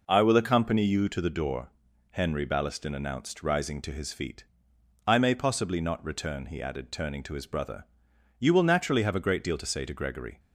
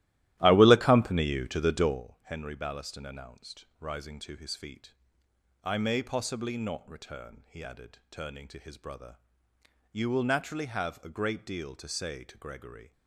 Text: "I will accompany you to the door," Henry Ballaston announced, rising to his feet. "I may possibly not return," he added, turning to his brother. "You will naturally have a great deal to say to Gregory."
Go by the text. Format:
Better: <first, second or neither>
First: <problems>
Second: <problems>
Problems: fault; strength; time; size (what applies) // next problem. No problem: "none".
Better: first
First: none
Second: starts louder than the rest; strong; until 2.1 s; 14 dB